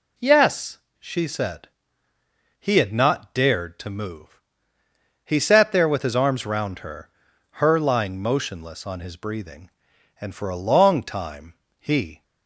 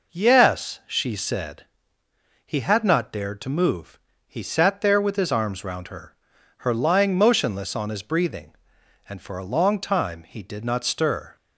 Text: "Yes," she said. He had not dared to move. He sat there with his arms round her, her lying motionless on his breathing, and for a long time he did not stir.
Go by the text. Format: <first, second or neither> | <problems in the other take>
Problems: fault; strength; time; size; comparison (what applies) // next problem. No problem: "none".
second | pauses between "time" and "he"; slight; at 11.5 s; 0.26 s long // stops before "did not stir"; at 12.2 s